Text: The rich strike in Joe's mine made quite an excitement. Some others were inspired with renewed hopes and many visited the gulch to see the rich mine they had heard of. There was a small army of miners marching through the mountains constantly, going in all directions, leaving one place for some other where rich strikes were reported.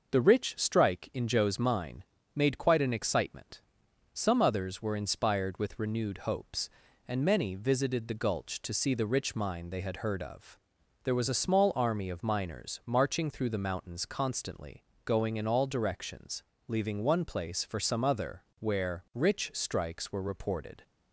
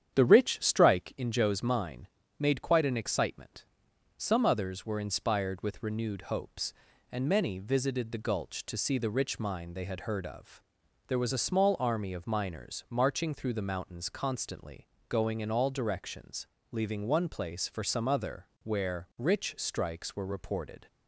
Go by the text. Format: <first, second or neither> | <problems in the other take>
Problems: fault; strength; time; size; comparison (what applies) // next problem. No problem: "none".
first | starts louder than the rest; strong; until 1.2 s; 9 dB // pauses between "mine" and "made"; slight; at 2.0 s; 0.28 s long; slight in the first // pauses between "other" and "where"; slight; at 18.4 s; 0.18 s long; slight in the first